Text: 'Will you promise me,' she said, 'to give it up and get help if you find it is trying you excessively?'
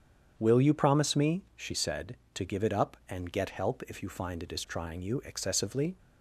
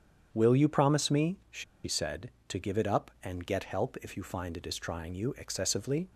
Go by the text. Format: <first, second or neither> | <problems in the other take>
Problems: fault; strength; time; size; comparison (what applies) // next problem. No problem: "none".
first | starts louder than the rest; strong; until 1.3 s; 8 dB; strong in the first // pauses between "she" and "said"; slight; at 1.6 s; 0.21 s long